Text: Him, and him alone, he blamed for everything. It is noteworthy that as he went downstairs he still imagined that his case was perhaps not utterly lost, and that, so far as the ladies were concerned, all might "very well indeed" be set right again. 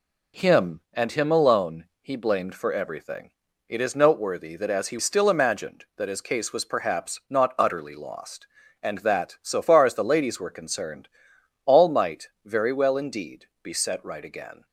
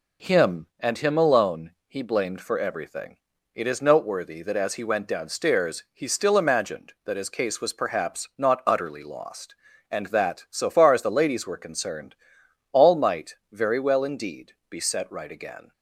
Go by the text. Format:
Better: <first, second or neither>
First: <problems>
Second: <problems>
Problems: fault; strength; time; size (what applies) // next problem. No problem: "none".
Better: second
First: skips "went downstairs he"; at 4.9 s // pauses between "indeed" and "be"; slight; at 13.4 s; 0.16 s long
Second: pauses between "indeed" and "be"; slight; at 14.5 s; 0.16 s long